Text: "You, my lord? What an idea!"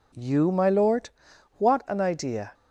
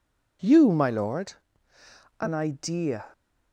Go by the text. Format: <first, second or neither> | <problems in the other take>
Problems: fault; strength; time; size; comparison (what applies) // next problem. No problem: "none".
first | skips "What"; at 1.7 s